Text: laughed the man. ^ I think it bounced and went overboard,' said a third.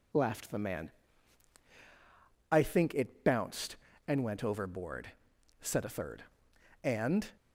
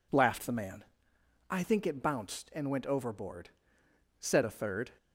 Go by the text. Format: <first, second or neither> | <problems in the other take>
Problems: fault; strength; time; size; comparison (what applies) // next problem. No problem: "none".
second | goes on to say "And"; slight; from 6.8 s on; 0.44 s long